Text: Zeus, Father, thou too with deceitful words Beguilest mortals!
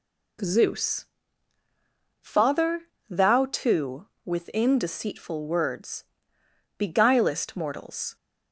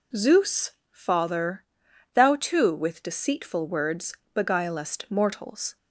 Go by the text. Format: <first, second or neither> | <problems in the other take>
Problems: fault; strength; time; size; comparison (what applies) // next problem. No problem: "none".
second | says "within" for "with"; at 4.2 s // pauses between "words" and "Beguilest"; noticeable; at 6.0 s; 0.72 s long; slight in the second